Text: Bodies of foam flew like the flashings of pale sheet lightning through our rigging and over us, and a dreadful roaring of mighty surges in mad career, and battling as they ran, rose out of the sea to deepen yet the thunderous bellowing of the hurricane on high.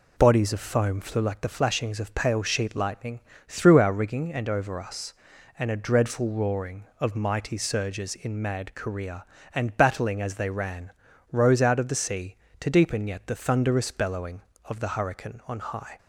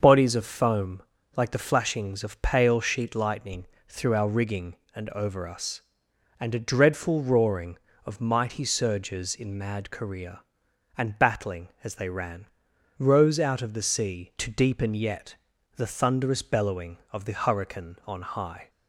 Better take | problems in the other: first | starts louder than the rest; until 1.0 s; 6.5 dB // skips "flew"; at 1.2 s // pauses between "lightning" and "through"; slight; at 3.6 s; 0.20 s long; slight in the first // pauses between "yet" and "the"; at 15.3 s; 0.40 s long

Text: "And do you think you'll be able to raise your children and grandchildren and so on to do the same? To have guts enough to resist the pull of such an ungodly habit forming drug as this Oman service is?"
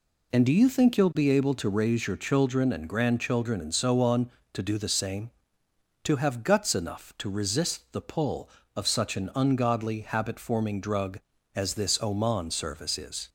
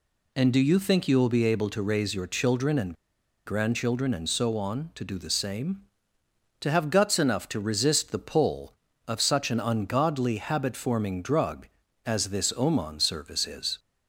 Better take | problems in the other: first | pauses between "and" and "grandchildren"; noticeable; at 2.9 s; 0.51 s long

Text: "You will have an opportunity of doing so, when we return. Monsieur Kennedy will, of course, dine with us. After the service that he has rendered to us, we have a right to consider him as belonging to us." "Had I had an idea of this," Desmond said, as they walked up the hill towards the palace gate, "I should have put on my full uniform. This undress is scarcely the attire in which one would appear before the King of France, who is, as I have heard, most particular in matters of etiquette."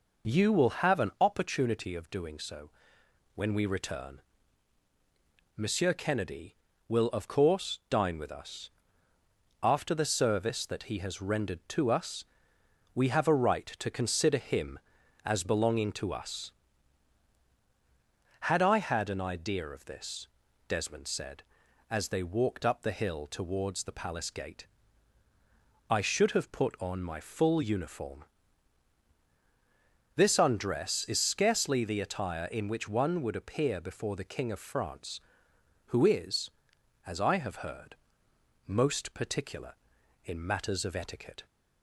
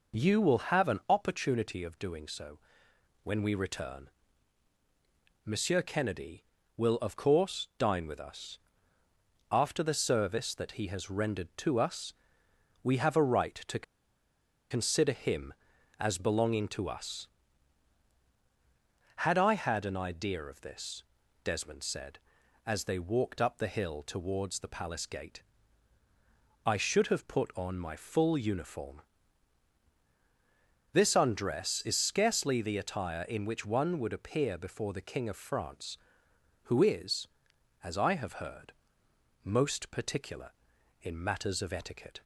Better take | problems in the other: first | pauses between "to" and "consider"; noticeable; at 13.8 s; 0.87 s long

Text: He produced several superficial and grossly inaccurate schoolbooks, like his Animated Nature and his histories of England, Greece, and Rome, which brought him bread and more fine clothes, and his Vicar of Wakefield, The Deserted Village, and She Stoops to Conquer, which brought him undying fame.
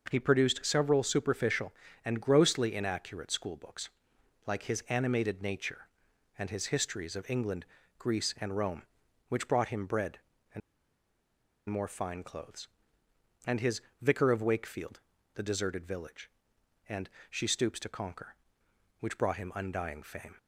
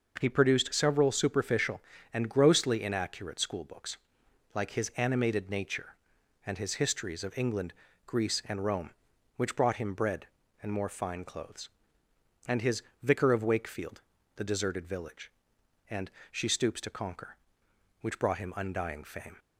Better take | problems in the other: second | pauses between "and" and "more"; at 10.6 s; 1.0 s long // pauses between "his" and "Vicar"; slight; at 13.8 s; 0.20 s long; slight in the second // pauses between "and" and "She"; slight; at 17.0 s; 0.22 s long; slight in the second

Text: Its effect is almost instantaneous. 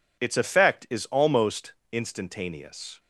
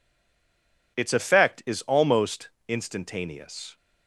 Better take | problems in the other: first | stays silent before the first word; slight; until 0.9 s; 0.9 s long // pauses between "almost" and "instantaneous"; slight; at 2.4 s; 0.18 s long; slight in the first

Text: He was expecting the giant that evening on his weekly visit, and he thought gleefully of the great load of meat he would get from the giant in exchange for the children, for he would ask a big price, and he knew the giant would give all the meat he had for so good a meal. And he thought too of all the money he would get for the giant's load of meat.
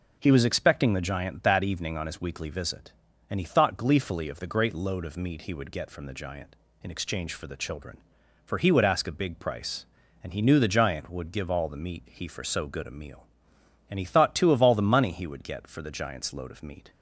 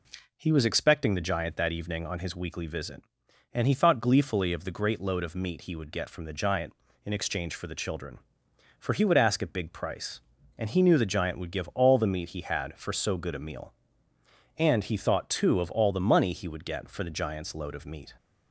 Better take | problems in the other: second | skips "had"; at 12.2 s

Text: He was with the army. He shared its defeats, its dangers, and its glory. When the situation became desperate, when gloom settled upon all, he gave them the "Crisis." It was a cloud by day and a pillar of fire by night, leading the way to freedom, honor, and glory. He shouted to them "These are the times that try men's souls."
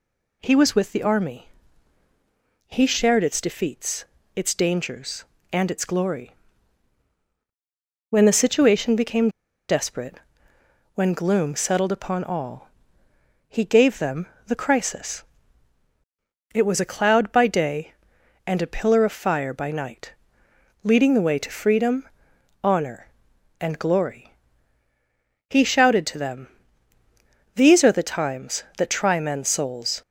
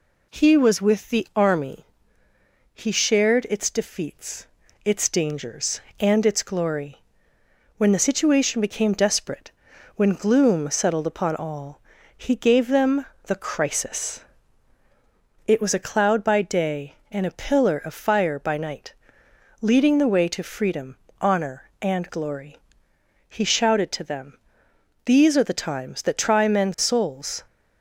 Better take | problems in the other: second | pauses between "became" and "desperate"; at 9.2 s; 0.39 s long // pauses between "them" and "the"; slight; at 14.2 s; 0.22 s long; slight in the second // pauses between "them" and "These"; at 26.4 s; 1.0 s long; noticeable in the second

